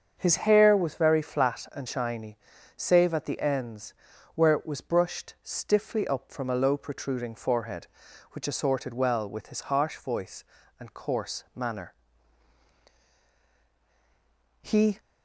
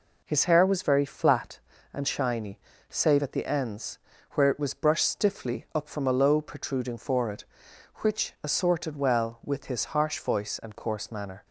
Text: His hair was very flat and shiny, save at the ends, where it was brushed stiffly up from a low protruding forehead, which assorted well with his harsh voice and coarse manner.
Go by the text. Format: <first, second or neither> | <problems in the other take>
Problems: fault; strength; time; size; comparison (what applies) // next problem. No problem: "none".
second | starts louder than the rest; until 1.1 s; 7 dB // goes on to say "He"; slight; from 14.6 s on; 0.38 s long